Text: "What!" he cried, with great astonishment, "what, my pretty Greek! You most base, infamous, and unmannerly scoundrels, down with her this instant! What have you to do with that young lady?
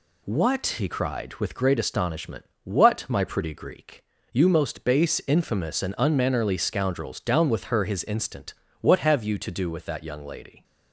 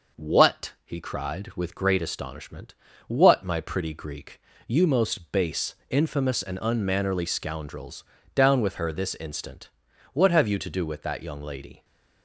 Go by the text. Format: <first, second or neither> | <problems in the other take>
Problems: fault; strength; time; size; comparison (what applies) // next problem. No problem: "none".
second | says "his" for "this"; at 7.8 s